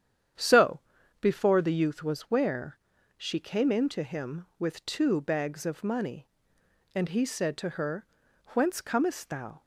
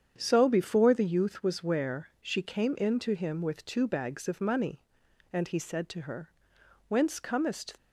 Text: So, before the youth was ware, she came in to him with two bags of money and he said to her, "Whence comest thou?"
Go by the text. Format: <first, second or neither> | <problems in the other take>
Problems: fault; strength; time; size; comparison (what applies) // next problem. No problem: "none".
first | starts louder than the rest; strong; until 1.1 s; 8 dB; strong in the first // stops before "thou"; at 7.7 s